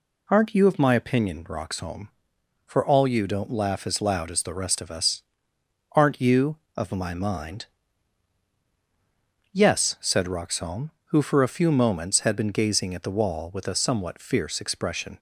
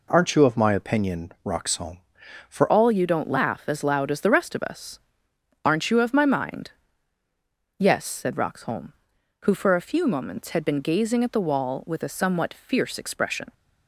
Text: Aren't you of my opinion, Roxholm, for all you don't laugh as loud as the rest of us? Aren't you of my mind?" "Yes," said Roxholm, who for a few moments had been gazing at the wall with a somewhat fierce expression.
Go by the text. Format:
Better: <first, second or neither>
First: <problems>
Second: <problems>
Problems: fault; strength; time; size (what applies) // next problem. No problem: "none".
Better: first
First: none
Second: changes voice at "all"; from 2.6 s on; 10.9 s long